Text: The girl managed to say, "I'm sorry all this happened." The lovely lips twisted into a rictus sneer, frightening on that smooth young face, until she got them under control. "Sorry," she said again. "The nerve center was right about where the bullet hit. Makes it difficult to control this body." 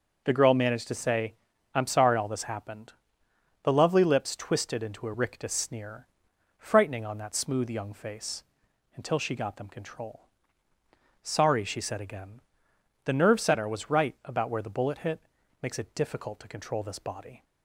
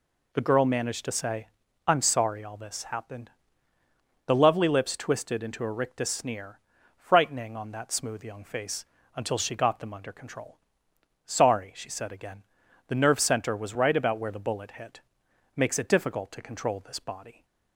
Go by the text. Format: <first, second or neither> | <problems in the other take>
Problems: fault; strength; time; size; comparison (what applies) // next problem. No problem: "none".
second | starts louder than the rest; noticeable; until 1.2 s; 6 dB // skips "under"; at 9.6 s